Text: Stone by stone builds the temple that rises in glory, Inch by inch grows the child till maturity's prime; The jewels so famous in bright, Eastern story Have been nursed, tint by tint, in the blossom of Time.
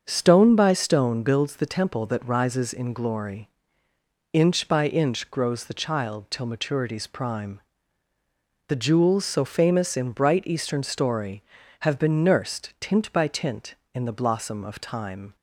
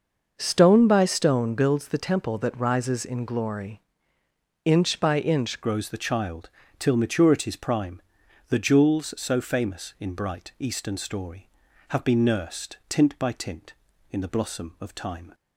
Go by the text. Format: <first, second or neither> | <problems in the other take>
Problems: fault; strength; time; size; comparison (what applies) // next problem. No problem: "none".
first | starts louder than the rest; noticeable; until 1.3 s; 6 dB; also in the first // changes voice at "grows"; from 5.6 s on; 9.7 s long // pauses between "child" and "till"; slight; at 6.4 s; 0.30 s long